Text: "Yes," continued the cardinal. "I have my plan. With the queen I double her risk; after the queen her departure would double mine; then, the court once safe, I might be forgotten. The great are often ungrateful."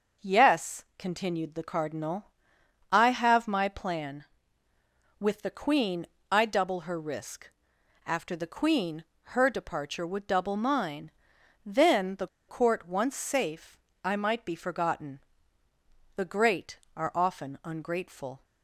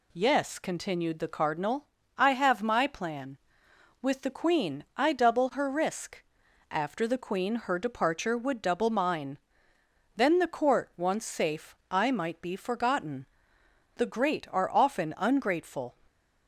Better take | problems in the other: second | pauses between "queen" and "I"; slight; at 6.0 s; 0.22 s long // pauses between "queen" and "her"; slight; at 9.0 s; 0.26 s long // pauses between "the" and "court"; slight; at 12.2 s; 0.21 s long

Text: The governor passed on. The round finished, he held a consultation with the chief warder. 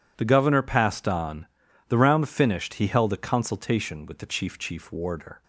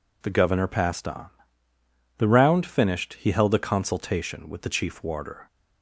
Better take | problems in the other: second | says "chief" twice; at 4.5 s

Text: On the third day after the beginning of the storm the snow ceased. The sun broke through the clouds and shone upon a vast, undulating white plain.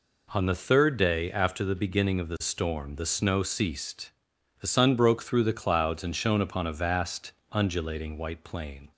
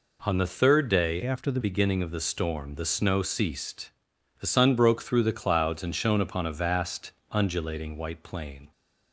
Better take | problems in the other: first | changes voice from "after" to "the"; from 1.2 to 1.6 s; 0.4 s long

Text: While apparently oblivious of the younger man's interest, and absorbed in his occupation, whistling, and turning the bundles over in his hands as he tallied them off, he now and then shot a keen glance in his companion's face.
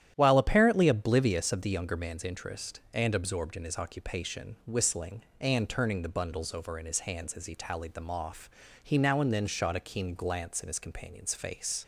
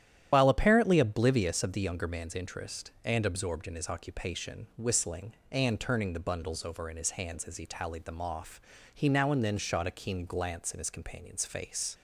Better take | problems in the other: first | loses the start of "While"; at 0.3 s; 60 ms // starts louder than the rest; strong; until 1.3 s; 11 dB; strong in the first

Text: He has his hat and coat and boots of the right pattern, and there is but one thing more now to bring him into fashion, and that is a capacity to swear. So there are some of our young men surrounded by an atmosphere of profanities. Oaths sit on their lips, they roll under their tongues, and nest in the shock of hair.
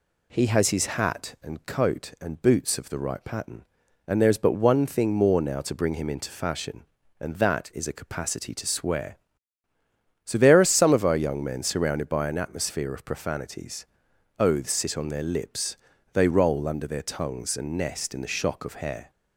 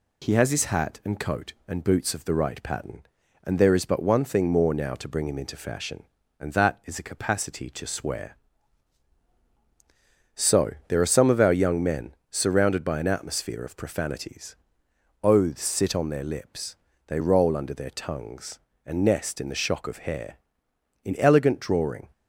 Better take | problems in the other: first | pauses between "men" and "surrounded"; slight; at 12.1 s; 0.16 s long // goes on to say "In elegant drawing"; noticeable; from 21.0 s on; 1.0 s long

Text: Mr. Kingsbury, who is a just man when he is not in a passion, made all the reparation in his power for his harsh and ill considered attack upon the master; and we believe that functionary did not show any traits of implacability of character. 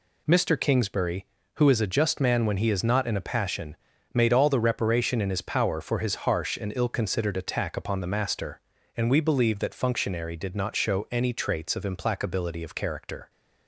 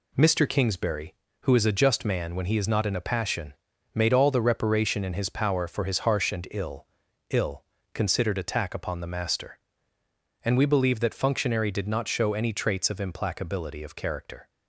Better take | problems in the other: first | says "ill" twice; at 7.3 s

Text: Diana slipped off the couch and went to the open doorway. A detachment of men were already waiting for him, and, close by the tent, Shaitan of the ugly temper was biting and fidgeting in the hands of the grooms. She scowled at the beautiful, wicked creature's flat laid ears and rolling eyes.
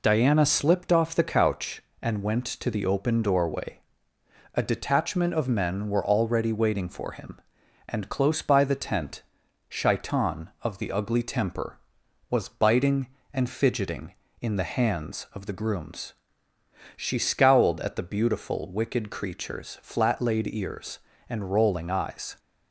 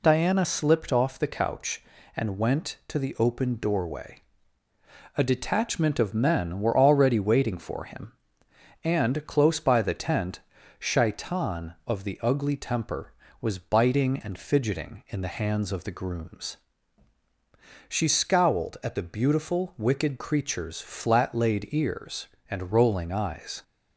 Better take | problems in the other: neither | none

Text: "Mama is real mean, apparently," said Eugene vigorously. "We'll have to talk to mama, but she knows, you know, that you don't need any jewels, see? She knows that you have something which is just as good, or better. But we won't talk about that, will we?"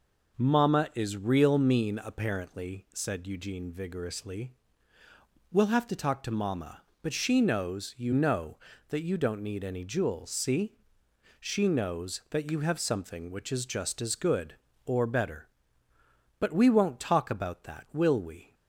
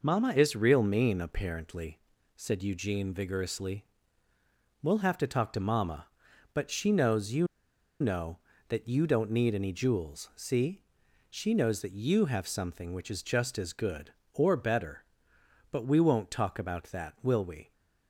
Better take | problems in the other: first | pauses between "you" and "know"; noticeable; at 7.4 s; 0.54 s long

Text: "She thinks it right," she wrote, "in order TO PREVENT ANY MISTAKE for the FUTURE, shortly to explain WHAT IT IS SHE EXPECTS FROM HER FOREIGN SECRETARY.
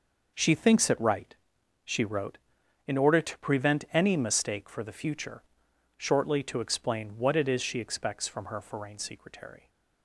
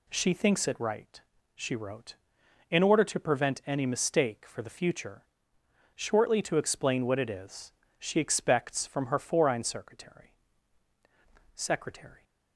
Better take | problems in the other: first | pauses between "IS" and "SHE"; slight; at 7.7 s; 0.26 s long // says "SECRETARY" twice; at 11.5 s

